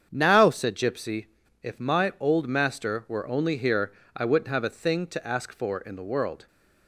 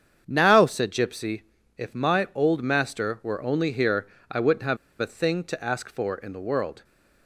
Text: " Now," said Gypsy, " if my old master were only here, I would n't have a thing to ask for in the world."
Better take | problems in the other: first | starts louder than the rest; strong; until 1.2 s; 8 dB; strong in the first // pauses between "have" and "a"; slight; at 4.7 s; 0.24 s long

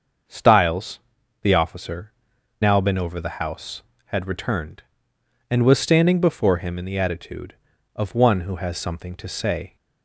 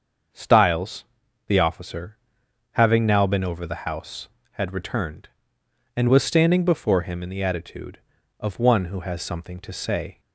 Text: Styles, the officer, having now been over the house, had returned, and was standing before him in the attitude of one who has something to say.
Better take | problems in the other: second | starts louder than the rest; until 1.7 s; 6.5 dB; also in the second // skips "having"; at 2.3 s

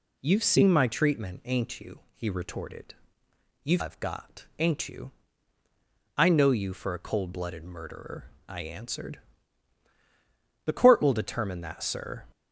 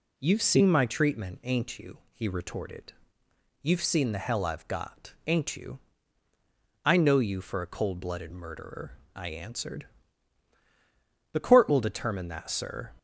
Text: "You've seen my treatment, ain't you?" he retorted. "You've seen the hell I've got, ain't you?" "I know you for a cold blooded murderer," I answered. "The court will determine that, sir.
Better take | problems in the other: second | skips "seen the hell"; at 3.8 s

